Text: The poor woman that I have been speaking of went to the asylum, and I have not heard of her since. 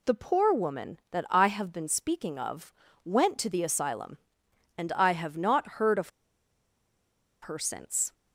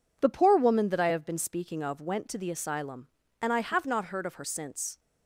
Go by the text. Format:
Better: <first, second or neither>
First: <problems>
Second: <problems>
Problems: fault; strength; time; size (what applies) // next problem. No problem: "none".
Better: second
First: pauses between "of" and "went"; slight; at 2.7 s; 0.32 s long // pauses between "of" and "her"; strong; at 6.0 s; 1.3 s long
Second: none